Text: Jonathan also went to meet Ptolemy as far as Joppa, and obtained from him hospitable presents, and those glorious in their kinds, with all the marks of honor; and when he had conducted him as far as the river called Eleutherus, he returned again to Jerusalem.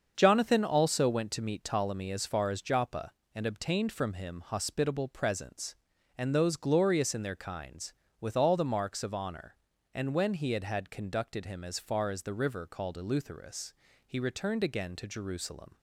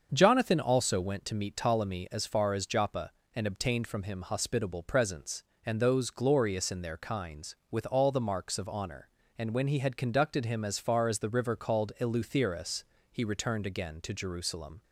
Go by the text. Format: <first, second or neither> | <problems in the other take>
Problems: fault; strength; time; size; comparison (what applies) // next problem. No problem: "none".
second | starts louder than the rest; until 1.1 s; 7 dB; also in the second // says "had" twice; at 10.6 s